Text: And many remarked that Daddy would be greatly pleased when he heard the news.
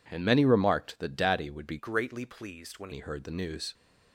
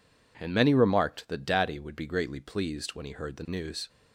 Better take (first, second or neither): second